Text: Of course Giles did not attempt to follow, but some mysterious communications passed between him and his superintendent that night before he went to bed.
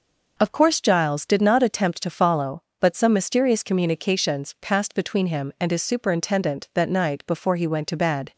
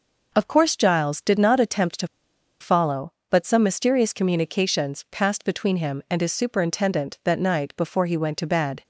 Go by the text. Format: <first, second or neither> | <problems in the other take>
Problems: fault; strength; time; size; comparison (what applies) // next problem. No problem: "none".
first | pauses between "to" and "follow"; noticeable; at 2.0 s; 0.54 s long